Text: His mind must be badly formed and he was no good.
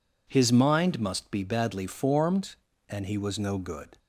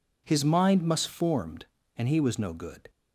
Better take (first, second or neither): first